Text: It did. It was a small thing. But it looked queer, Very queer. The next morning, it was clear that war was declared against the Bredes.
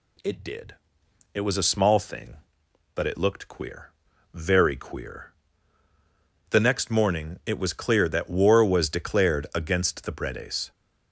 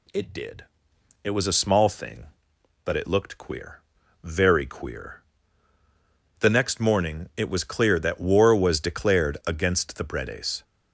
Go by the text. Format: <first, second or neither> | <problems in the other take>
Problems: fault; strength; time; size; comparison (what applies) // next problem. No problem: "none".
neither | none